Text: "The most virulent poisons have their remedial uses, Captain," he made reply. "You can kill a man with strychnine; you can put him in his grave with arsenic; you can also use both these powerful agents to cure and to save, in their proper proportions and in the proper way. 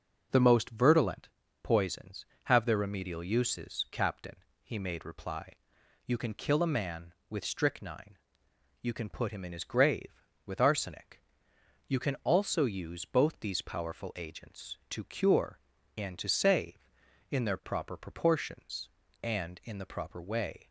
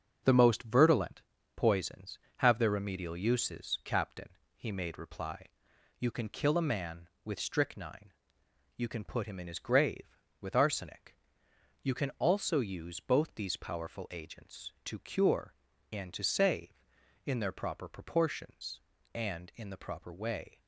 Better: first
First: starts louder than the rest; until 1.6 s; 6.5 dB // pauses between "virulent" and "poisons"; slight; at 1.2 s; 0.34 s long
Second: gets quieter; noticeable; throughout; 6 dB // starts louder than the rest; strong; until 1.5 s; 7 dB // pauses between "virulent" and "poisons"; slight; at 1.2 s; 0.34 s long

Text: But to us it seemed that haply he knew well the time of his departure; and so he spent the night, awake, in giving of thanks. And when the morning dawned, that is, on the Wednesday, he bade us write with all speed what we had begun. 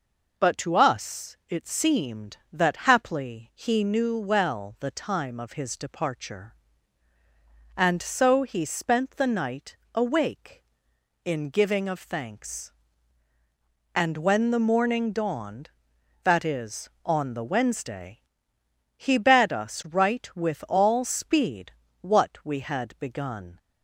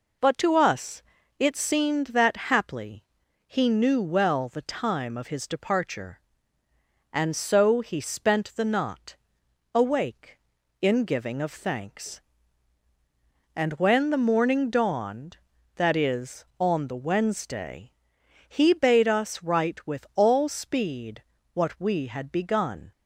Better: first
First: pauses between "speed" and "what"; slight; at 21.7 s; 0.30 s long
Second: pauses between "us" and "it"; slight; at 1.0 s; 0.36 s long // pauses between "haply" and "he"; at 3.0 s; 0.42 s long // says "knot" for "night"; at 8.6 s // pauses between "speed" and "what"; slight; at 21.2 s; 0.32 s long

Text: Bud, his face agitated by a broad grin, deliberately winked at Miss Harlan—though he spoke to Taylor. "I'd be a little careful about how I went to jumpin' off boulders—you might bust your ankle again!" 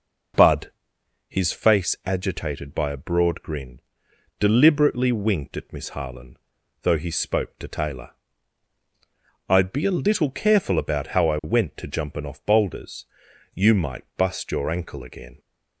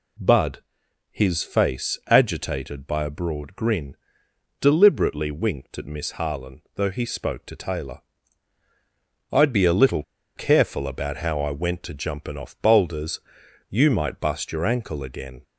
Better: first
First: none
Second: pauses between "little" and "careful"; slight; at 10.0 s; 0.33 s long

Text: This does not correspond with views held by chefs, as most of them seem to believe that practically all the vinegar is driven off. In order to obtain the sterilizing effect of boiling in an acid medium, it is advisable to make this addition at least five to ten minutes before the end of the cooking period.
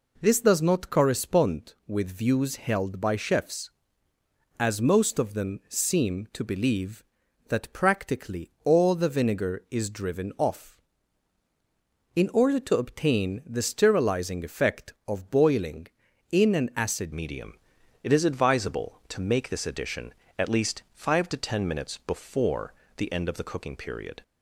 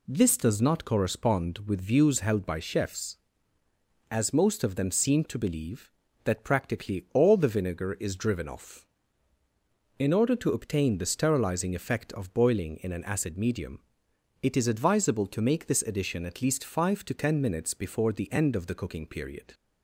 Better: second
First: changes voice at "medium"; from 17.1 s on; 7.1 s long // pauses between "before" and "the"; slight; at 22.7 s; 0.26 s long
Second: none

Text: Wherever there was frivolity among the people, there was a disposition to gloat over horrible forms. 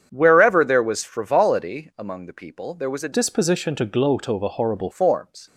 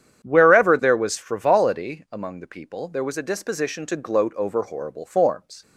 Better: second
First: starts louder than the rest; strong; until 1.1 s; 8 dB // changes voice from "disposition" to "horrible"; from 3.1 to 4.9 s; 1.8 s long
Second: starts louder than the rest; strong; until 1.2 s; 9 dB

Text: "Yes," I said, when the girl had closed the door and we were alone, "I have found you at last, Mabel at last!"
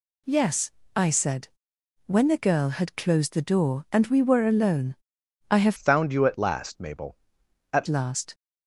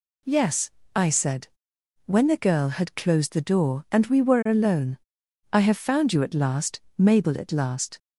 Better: second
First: changes voice from "found" to "at"; from 5.7 to 7.8 s; 2.1 s long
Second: none

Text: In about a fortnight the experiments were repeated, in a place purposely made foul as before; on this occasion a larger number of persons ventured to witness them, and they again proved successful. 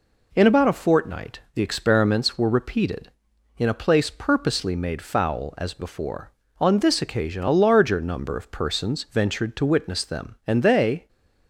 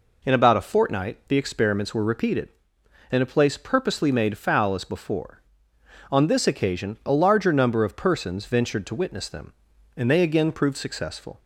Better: second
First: pauses between "fortnight" and "the"; slight; at 1.3 s; 0.16 s long // stops before "again proved successful"; at 11.0 s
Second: none

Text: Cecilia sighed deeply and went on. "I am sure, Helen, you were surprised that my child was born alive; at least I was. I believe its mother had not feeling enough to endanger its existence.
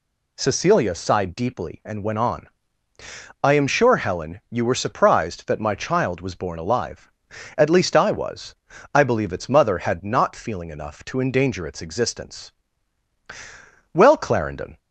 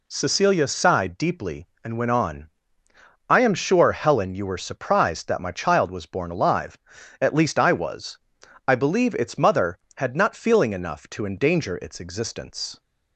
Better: second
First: goes on to say "Well Clarendon"; noticeable; from 13.9 s on; 0.86 s long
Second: none

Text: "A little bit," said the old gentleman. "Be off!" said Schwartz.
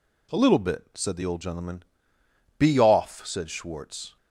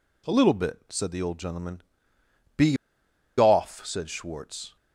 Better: first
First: none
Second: pauses between "Be" and "off"; noticeable; at 2.7 s; 0.63 s long

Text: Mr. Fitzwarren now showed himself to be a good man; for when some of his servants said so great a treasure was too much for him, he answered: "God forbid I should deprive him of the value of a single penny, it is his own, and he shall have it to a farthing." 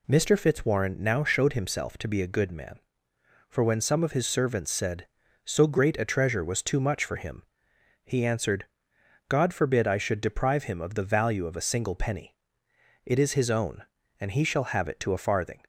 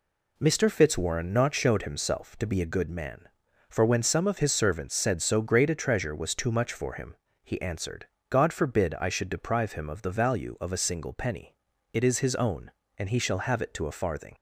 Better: first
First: none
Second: says "not" for "now"; at 1.3 s

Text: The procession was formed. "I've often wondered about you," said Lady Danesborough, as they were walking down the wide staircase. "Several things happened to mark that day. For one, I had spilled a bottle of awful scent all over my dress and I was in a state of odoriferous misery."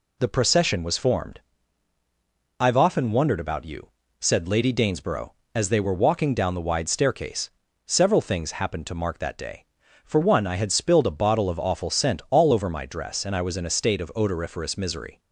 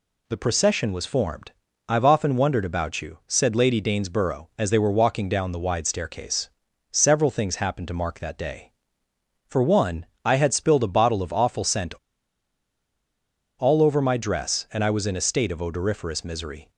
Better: first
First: none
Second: pauses between "scent" and "all"; strong; at 11.9 s; 1.6 s long

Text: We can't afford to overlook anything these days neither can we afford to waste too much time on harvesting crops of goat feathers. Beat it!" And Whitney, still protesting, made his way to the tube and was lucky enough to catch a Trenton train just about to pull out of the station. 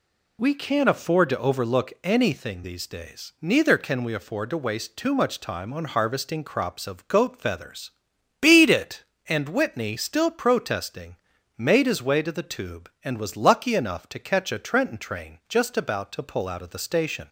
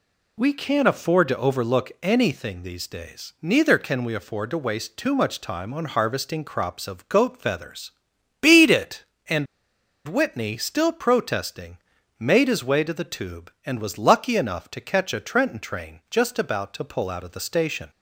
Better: first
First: none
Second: pauses between "And" and "Whitney"; noticeable; at 9.4 s; 0.62 s long

